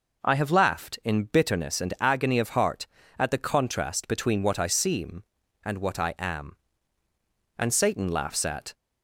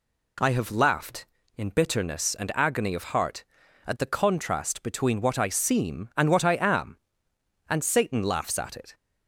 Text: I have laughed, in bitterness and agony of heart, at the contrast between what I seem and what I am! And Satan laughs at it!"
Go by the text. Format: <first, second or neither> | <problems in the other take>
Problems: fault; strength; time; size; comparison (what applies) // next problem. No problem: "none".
second | stops before "it"; at 8.7 s